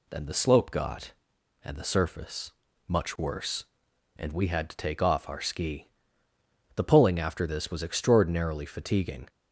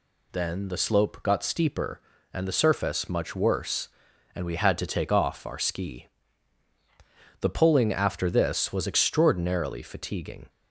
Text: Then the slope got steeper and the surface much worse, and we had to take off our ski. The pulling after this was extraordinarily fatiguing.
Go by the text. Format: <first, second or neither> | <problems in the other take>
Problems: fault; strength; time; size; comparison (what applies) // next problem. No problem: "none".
second | skips "steeper"; at 1.3 s // pauses between "surface" and "much"; slight; at 2.5 s; 0.36 s long